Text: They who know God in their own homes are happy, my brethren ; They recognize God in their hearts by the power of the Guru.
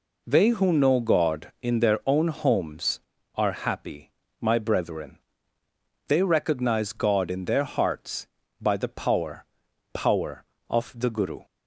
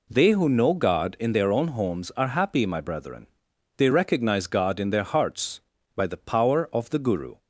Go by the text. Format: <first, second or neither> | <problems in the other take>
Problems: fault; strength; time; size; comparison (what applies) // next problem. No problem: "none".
second | says "power" twice; at 9.9 s